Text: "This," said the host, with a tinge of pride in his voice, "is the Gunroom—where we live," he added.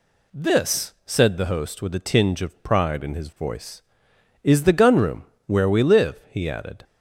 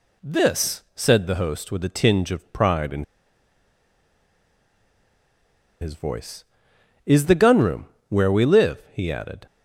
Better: first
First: none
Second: pauses between "in" and "his"; strong; at 3.0 s; 2.7 s long

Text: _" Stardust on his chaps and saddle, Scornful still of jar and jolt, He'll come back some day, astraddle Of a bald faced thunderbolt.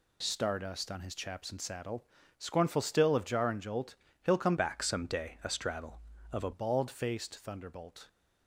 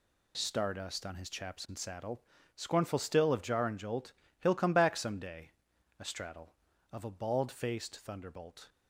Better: second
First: changes voice from "back" to "a"; from 4.5 to 6.5 s; 2.0 s long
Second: none

